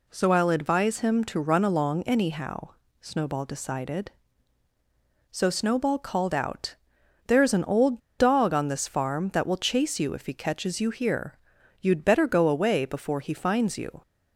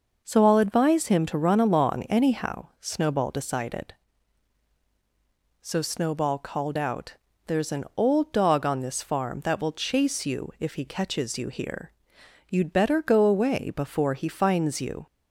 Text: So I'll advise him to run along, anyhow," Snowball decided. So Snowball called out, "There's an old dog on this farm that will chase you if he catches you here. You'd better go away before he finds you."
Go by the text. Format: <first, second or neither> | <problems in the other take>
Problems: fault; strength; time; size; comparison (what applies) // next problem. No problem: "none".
second | pauses between "old" and "dog"; slight; at 7.9 s; 0.19 s long